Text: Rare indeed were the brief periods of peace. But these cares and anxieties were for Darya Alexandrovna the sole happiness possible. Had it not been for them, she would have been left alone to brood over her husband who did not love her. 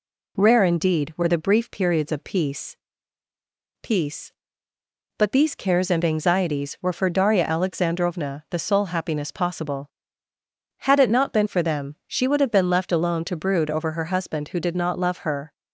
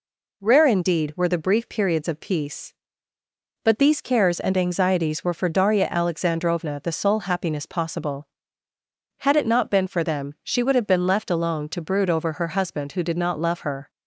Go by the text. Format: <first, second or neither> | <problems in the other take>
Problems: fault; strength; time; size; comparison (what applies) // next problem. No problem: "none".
second | says "peace" twice; at 3.8 s